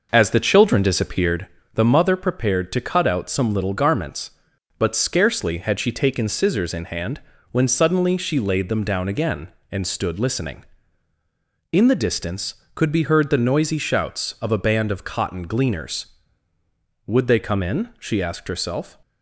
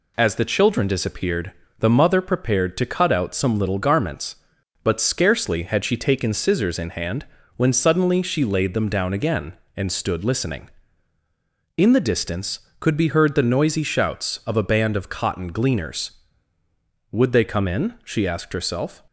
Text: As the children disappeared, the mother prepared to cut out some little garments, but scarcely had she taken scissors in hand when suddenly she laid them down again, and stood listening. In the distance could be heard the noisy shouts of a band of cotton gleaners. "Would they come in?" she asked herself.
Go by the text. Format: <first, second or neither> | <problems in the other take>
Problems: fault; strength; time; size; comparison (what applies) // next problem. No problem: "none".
second | starts louder than the rest; noticeable; until 1.4 s; 5.5 dB // pauses between "hand" and "when"; slight; at 7.2 s; 0.30 s long; slight in the second